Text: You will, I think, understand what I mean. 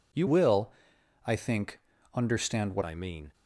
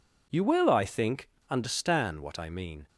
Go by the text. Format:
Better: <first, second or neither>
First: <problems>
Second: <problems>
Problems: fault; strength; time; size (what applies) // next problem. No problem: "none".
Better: second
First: changes voice from "will" to "what"; from 0.2 to 2.8 s; 2.6 s long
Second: none